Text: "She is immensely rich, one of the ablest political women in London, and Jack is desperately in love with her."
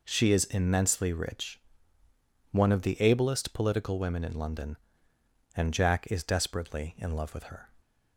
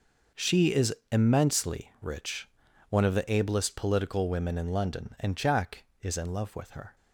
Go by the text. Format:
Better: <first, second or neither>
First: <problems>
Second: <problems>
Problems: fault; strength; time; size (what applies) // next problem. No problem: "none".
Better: first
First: none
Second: pauses between "is" and "immensely"; slight; at 0.9 s; 0.16 s long // skips "desperately"; at 6.1 s